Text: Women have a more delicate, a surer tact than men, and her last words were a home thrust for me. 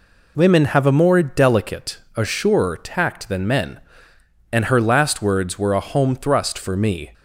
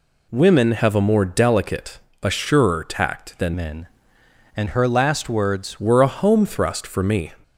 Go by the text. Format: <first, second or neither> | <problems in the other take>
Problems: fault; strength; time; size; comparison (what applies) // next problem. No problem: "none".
first | changes voice from "men" to "words"; from 3.5 to 5.7 s; 2.2 s long